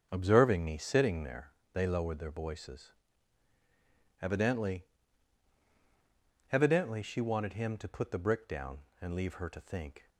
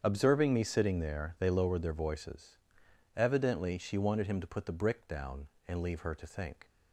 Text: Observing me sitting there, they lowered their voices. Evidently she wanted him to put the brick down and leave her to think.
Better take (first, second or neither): second